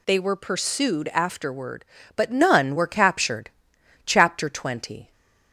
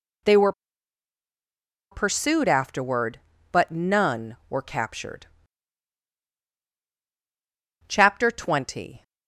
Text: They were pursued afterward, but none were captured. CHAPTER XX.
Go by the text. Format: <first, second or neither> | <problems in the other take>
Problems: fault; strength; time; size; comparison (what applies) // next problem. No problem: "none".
first | pauses between "were" and "pursued"; strong; at 0.5 s; 1.4 s long